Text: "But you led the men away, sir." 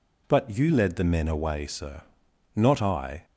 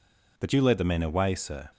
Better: second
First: goes on to say "Not I"; noticeable; from 2.5 s on; 0.70 s long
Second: none

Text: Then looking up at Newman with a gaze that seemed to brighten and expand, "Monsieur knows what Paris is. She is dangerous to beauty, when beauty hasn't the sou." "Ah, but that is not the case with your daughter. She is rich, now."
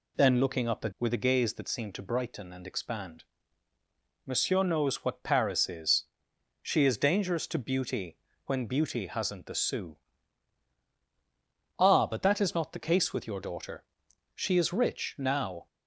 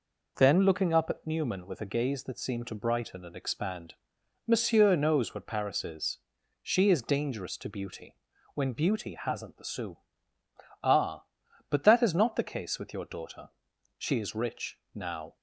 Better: second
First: skips "Newman"; at 0.9 s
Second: none

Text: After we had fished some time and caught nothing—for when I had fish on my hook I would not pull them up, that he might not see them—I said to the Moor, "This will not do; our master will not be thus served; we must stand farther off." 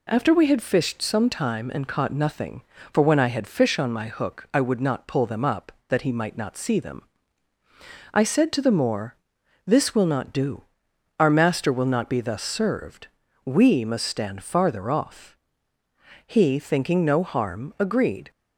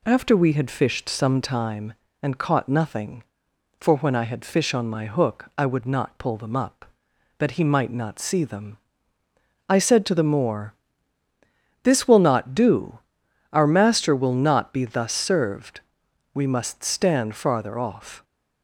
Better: second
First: goes on to say "He thinking no harm agreed"; strong; from 16.2 s on; 2.0 s long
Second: none

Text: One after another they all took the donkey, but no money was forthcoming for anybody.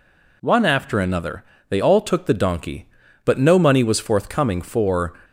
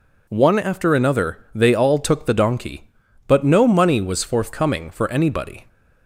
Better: second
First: pauses between "another" and "they"; slight; at 1.4 s; 0.26 s long // stops before "anybody"; at 5.2 s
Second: pauses between "another" and "they"; slight; at 1.3 s; 0.16 s long

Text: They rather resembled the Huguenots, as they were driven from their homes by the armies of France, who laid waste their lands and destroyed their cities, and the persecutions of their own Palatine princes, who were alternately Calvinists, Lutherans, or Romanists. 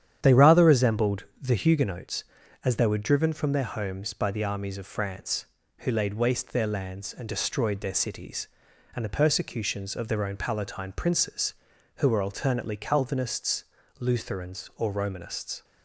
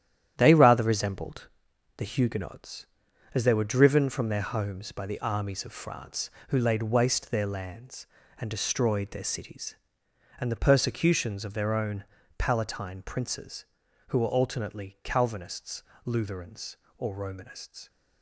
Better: first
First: starts louder than the rest; strong; until 1.2 s; 9.5 dB // pauses between "resembled" and "the"; slight; at 1.2 s; 0.18 s long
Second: gets quieter; strong; throughout; 8 dB // starts louder than the rest; strong; until 1.3 s; 10.5 dB // pauses between "resembled" and "the"; noticeable; at 1.4 s; 0.48 s long // pauses between "own" and "Palatine"; slight; at 12.0 s; 0.32 s long

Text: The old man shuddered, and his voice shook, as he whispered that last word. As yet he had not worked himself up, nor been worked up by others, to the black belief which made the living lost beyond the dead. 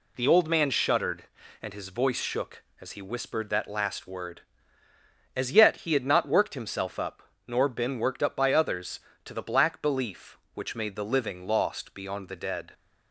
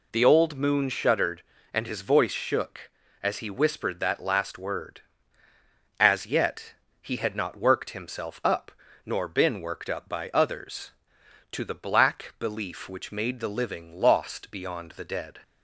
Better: first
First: none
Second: says "moon" for "man"; at 0.5 s // pauses between "yet" and "he"; slight; at 6.7 s; 0.28 s long

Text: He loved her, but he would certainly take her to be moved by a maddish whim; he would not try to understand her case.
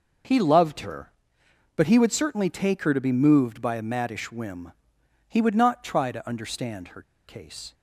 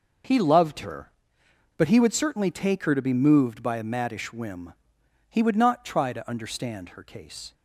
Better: second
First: pauses between "her" and "case"; slight; at 7.0 s; 0.24 s long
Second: none

